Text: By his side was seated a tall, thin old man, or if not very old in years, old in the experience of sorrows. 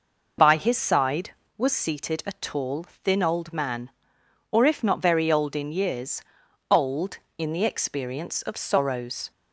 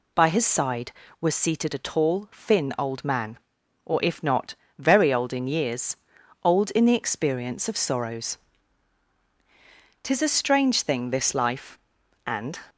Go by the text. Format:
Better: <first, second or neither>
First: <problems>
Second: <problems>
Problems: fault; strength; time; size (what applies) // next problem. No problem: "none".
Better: first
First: none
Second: pauses between "not" and "very"; slight; at 4.5 s; 0.22 s long // goes on to say "Tis a strange thing this life and"; strong; from 10.0 s on; 2.5 s long